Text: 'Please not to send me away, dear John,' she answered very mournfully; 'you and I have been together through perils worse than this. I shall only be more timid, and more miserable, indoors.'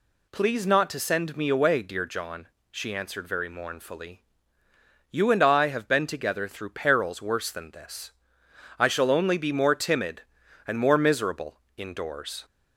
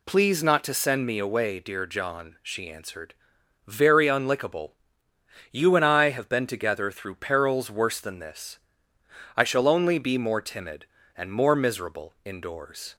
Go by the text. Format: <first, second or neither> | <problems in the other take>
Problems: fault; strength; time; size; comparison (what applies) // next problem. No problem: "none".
first | pauses between "answered" and "very"; noticeable; at 3.1 s; 0.52 s long // says "unlickable" for "mournfully"; at 4.0 s